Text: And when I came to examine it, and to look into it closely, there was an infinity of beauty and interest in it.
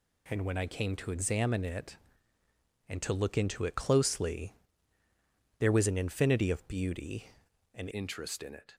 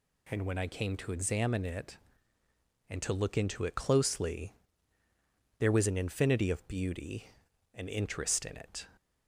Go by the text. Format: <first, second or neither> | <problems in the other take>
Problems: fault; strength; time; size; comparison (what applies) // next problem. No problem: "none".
second | changes voice at "interest"; from 7.9 s on; 0.8 s long